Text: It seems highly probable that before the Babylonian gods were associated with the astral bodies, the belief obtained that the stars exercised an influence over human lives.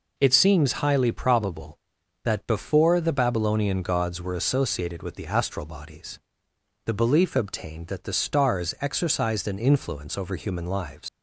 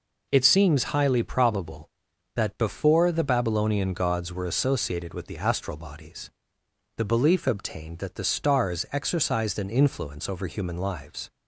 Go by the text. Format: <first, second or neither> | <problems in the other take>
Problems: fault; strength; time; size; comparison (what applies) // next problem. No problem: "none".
second | leaves "lives" unfinished; at 11.0 s; 105 ms